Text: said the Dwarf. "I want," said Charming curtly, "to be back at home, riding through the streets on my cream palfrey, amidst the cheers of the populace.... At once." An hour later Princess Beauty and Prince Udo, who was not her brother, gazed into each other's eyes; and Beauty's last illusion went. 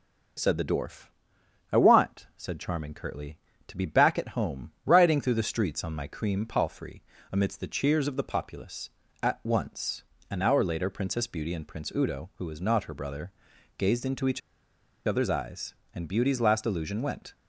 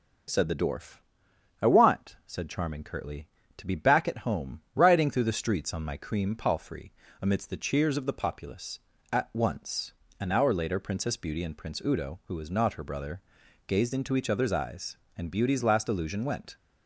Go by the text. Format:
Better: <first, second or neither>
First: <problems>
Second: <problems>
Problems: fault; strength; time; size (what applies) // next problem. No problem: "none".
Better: second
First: starts louder than the rest; until 2.0 s; 6 dB // pauses between "each" and "other's"; noticeable; at 14.4 s; 0.67 s long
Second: starts louder than the rest; until 1.9 s; 6 dB